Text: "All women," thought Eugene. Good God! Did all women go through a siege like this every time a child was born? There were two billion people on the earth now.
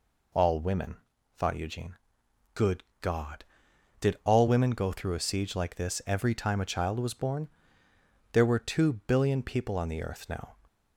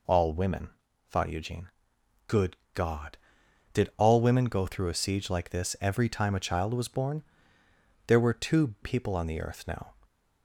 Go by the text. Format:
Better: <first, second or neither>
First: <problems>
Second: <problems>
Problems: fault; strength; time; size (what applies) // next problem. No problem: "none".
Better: first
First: pauses between "Good" and "God"; slight; at 2.8 s; 0.20 s long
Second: pauses between "Good" and "God"; slight; at 2.5 s; 0.20 s long // skips "billion"; at 8.7 s